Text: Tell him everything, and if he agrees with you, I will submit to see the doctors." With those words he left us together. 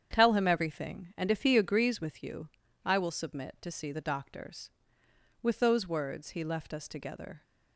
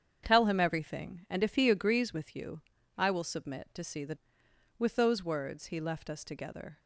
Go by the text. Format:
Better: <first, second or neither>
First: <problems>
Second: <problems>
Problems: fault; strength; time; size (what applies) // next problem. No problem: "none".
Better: first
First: starts louder than the rest; strong; until 1.1 s; 8.5 dB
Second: starts louder than the rest; strong; until 1.2 s; 8 dB // skips "doctors"; at 4.4 s